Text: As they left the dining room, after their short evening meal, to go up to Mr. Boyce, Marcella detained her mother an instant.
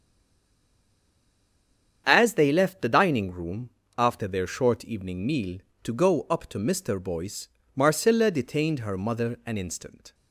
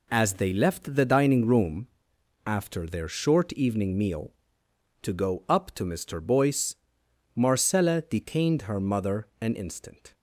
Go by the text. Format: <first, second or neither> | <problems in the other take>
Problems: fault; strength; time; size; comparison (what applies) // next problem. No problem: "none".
second | stays silent before the first word; noticeable; until 2.0 s; 2.0 s long // starts louder than the rest; strong; until 3.0 s; 8 dB